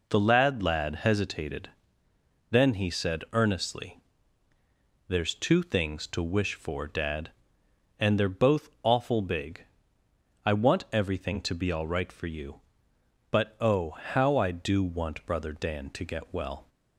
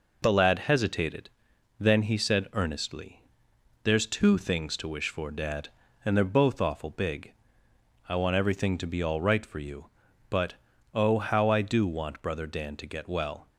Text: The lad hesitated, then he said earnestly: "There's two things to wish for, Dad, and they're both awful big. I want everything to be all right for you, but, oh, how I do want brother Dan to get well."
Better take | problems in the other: second | says "lad" twice; at 0.6 s // pauses between "both" and "awful"; slight; at 8.6 s; 0.16 s long

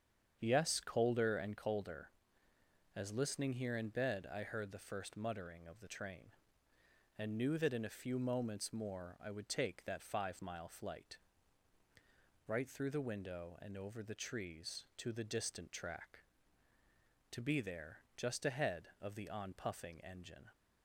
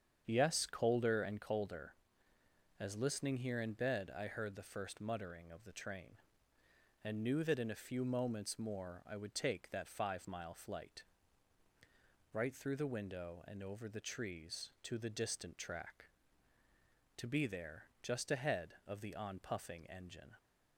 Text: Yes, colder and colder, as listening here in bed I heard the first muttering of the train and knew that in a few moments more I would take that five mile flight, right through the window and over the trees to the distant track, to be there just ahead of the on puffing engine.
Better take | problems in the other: neither | starts louder than the rest; strong; the same in both

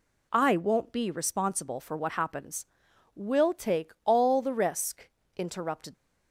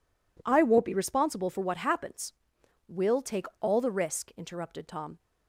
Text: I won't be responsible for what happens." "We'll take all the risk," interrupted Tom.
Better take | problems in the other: second | stops before "Tom"; at 5.9 s

